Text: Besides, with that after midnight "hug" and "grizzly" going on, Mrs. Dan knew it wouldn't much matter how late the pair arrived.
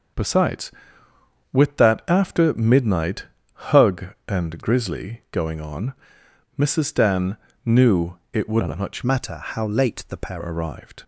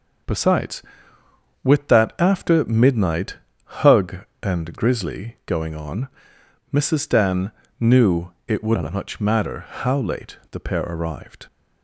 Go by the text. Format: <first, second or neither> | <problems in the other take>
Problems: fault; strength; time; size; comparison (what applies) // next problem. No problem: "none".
second | starts louder than the rest; until 1.9 s; 6 dB; noticeable in the second // pauses between "midnight" and "hug"; slight; at 3.2 s; 0.28 s long; slight in the second // pauses between "Dan" and "knew"; slight; at 7.3 s; 0.26 s long; slight in the second // pauses between "knew" and "it"; slight; at 8.1 s; 0.16 s long; slight in the second // changes voice from "matter" to "pair"; from 9.0 to 10.3 s; 1.3 s long